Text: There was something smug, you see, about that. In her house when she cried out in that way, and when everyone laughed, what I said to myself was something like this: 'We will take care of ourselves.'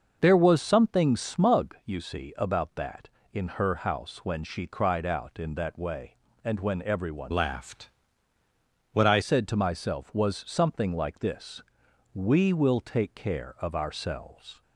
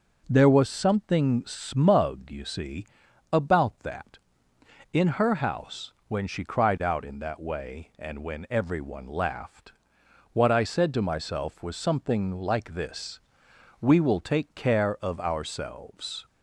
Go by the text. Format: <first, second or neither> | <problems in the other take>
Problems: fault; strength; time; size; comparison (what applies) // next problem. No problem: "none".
second | starts louder than the rest; noticeable; until 1.2 s; 6 dB // changes voice from "laughed" to "I"; from 7.3 to 9.2 s; 1.9 s long